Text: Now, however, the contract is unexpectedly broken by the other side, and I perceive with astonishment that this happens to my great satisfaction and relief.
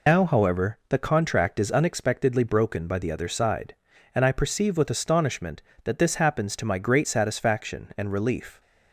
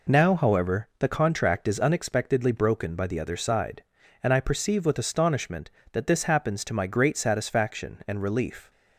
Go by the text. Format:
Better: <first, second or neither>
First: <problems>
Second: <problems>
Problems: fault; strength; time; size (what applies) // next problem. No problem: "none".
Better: second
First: loses the start of "Now"; at 0.0 s; 95 ms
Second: none